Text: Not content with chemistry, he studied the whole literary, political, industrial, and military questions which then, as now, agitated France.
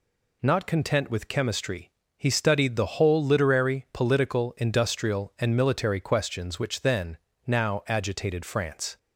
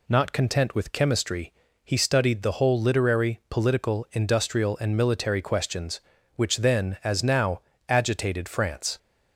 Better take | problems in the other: second | skips "as"; at 7.3 s

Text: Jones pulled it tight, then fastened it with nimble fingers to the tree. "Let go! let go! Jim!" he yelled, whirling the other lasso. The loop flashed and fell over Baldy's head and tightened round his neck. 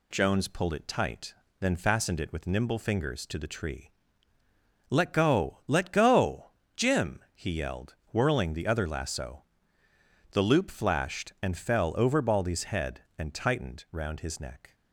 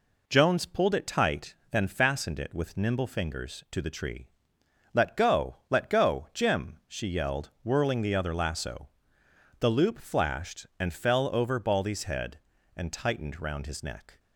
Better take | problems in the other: first | says "she" for "he"; at 6.8 s

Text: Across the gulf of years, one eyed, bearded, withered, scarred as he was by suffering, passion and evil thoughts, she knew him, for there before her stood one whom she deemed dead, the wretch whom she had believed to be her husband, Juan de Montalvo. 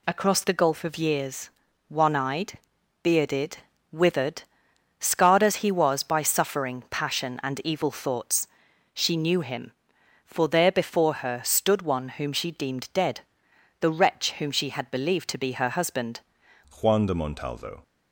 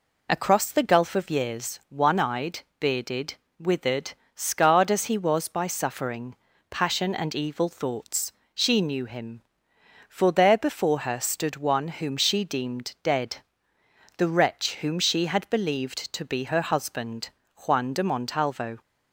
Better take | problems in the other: second | changes voice at "Juan"; from 16.8 s on; 1.0 s long

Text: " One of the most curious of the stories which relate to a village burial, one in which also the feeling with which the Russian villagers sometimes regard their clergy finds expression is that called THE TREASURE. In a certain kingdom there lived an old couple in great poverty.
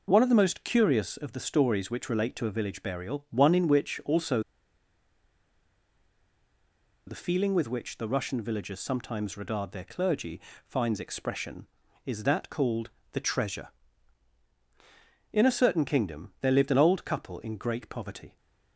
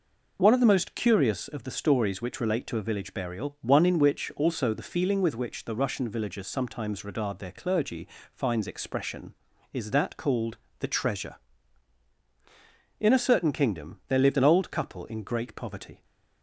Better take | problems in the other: second | pauses between "also" and "the"; strong; at 4.4 s; 2.6 s long // pauses between "clergy" and "finds"; slight; at 10.4 s; 0.24 s long; slight in the second // pauses between "called" and "THE"; slight; at 12.8 s; 0.22 s long; slight in the second

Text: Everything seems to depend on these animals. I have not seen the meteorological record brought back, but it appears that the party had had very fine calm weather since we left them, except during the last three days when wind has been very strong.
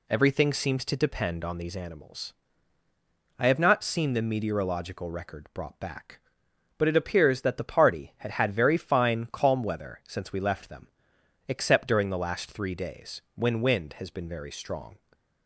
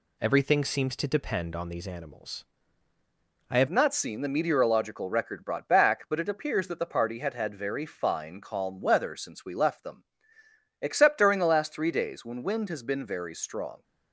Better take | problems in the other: first | changes voice at "not"; from 3.6 s on; 10.2 s long

